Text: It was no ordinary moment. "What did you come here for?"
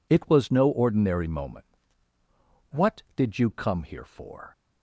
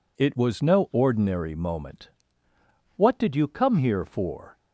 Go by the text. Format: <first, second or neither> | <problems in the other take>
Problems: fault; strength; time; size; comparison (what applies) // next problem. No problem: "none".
neither | none